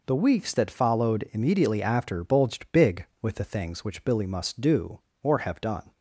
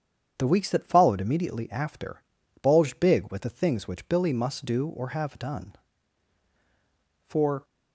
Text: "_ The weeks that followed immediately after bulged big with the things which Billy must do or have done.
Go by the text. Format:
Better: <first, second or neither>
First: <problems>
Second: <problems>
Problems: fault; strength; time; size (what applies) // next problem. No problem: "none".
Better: first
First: none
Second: starts louder than the rest; strong; until 1.3 s; 8 dB // pauses between "after" and "bulged"; at 2.2 s; 0.40 s long // goes on to say "For"; slight; from 7.2 s on; 0.36 s long